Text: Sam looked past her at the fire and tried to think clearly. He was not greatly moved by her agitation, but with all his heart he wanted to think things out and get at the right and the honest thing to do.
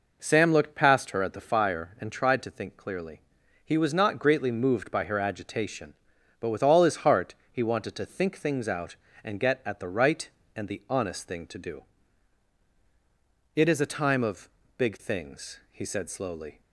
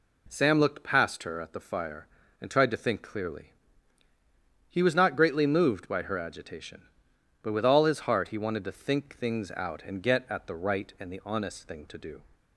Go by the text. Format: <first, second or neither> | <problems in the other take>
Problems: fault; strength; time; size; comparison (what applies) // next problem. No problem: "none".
second | pauses between "heart" and "he"; slight; at 7.3 s; 0.18 s long // goes on to say "It is a time of big things he said slowly"; strong; from 13.5 s on; 3.0 s long